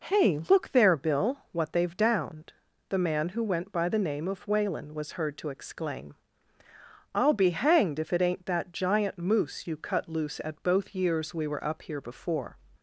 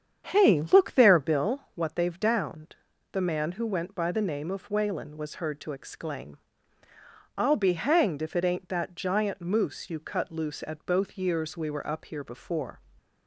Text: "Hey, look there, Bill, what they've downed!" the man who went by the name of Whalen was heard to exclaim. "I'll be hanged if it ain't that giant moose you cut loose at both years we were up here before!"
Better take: first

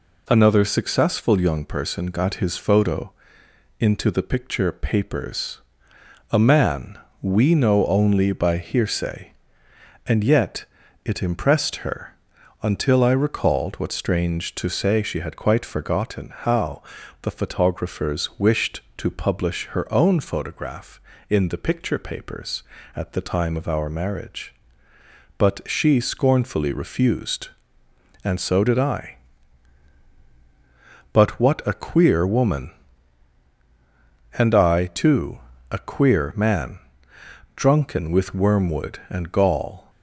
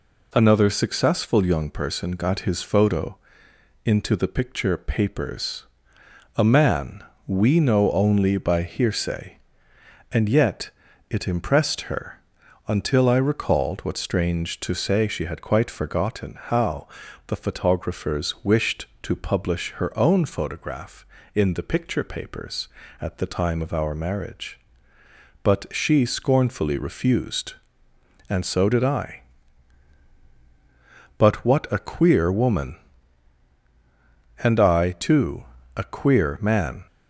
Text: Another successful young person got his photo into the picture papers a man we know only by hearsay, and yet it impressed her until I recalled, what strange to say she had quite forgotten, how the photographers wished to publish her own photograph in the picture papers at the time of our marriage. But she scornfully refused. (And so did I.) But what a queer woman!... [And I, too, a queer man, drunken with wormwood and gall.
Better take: first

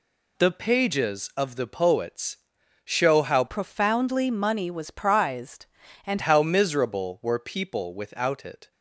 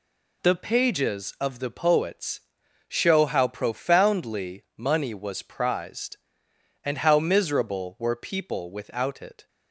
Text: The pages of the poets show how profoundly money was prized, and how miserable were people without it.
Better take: second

